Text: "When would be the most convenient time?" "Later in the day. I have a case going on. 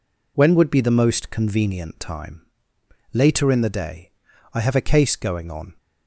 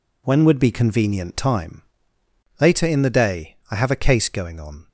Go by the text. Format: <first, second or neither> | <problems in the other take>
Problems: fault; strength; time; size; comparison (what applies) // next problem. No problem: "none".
first | skips "the most"; at 0.7 s